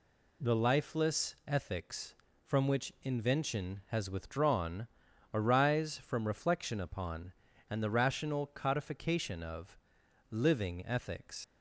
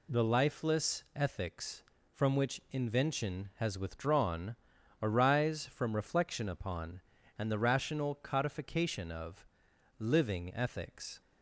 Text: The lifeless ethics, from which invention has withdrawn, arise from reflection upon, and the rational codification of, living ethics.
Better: second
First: leaves "ethics" unfinished; at 11.4 s; 75 ms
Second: none

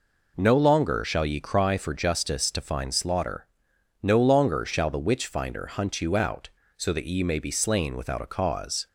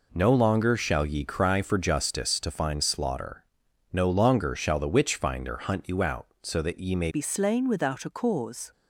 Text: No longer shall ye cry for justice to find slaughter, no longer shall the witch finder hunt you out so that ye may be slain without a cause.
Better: first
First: none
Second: changes voice at "be"; from 7.0 s on; 1.7 s long

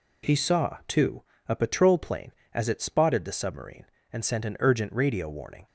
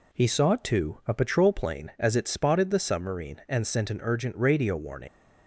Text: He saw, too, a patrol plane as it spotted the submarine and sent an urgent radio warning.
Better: first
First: none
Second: leaves "warning" unfinished; at 5.0 s; 90 ms

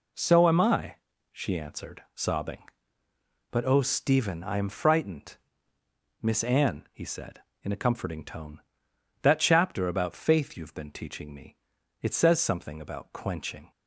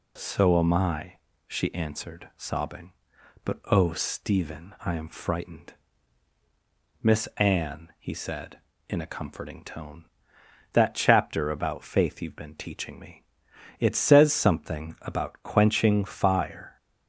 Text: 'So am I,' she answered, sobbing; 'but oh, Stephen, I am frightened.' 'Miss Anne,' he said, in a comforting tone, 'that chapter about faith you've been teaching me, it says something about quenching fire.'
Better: second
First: stops before "fire"; at 13.7 s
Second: none

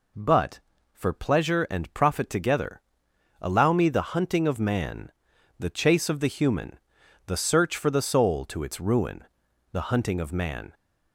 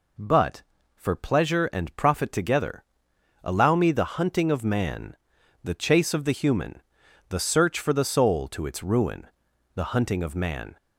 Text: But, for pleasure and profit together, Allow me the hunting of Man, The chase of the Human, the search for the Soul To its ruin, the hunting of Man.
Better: neither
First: none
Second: none

